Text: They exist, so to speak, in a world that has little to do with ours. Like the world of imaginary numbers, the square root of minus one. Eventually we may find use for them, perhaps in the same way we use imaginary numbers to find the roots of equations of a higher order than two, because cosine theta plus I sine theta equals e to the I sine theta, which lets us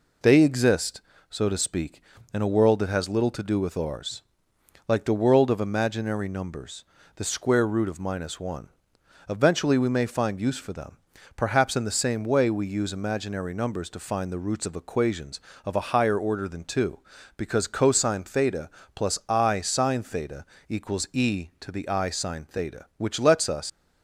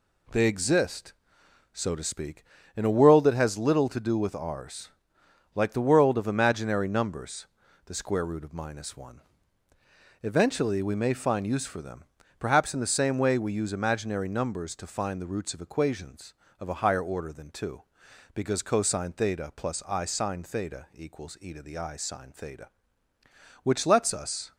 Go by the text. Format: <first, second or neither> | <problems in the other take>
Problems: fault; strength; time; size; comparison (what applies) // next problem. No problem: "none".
second | pauses between "theta" and "plus"; slight; at 18.6 s; 0.26 s long // pauses between "theta" and "equals"; slight; at 20.4 s; 0.22 s long // leaves "us" unfinished; at 23.6 s; 130 ms